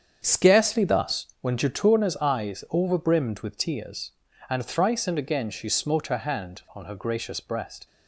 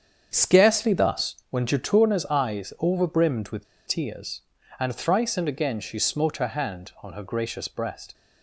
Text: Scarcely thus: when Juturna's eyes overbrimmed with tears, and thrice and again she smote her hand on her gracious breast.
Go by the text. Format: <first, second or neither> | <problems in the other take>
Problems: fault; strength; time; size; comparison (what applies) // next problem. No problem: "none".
first | starts louder than the rest; strong; until 1.3 s; 7.5 dB; strong in the first // pauses between "with" and "tears"; slight; at 3.6 s; 0.21 s long